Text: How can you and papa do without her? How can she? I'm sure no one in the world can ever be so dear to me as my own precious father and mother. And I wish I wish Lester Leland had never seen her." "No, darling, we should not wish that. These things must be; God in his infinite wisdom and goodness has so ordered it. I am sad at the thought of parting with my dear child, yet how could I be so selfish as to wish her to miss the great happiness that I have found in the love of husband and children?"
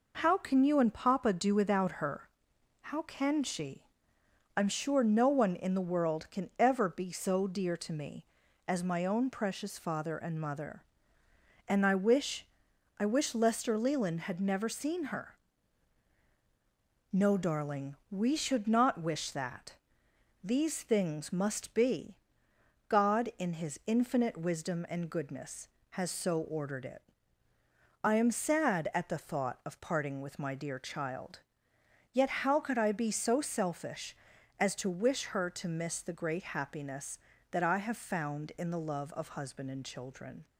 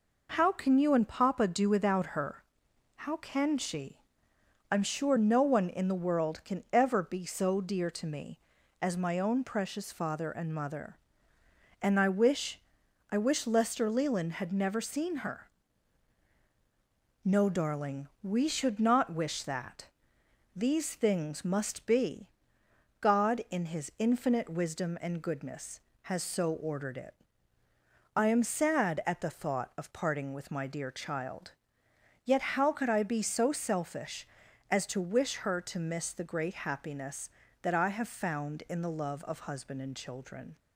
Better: neither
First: pauses between "wish" and "I"; noticeable; at 12.4 s; 0.51 s long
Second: pauses between "wish" and "I"; noticeable; at 12.5 s; 0.50 s long

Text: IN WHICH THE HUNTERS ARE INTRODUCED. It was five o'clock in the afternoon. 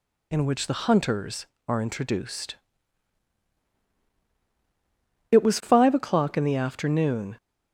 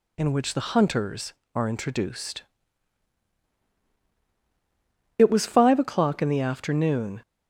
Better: neither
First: none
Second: none

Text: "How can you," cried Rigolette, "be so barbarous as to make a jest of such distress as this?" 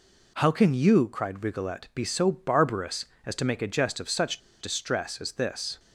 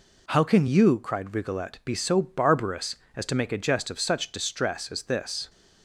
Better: second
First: pauses between "such" and "distress"; slight; at 4.3 s; 0.20 s long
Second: none

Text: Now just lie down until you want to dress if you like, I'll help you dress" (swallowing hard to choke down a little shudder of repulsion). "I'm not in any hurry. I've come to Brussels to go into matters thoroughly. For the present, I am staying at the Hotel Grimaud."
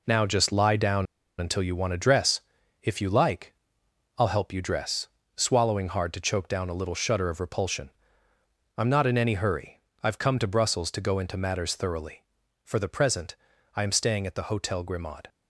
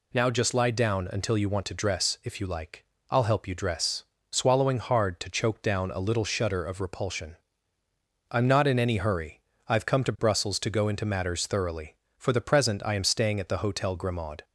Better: second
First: pauses between "down" and "until"; slight; at 1.0 s; 0.34 s long // pauses between "dress" and "if"; at 2.4 s; 0.42 s long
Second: none

